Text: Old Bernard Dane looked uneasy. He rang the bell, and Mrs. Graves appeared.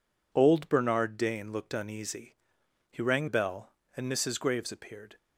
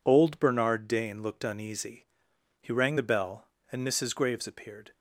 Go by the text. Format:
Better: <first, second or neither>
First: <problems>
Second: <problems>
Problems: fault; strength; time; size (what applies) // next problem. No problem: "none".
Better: second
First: skips "the"; at 3.2 s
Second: none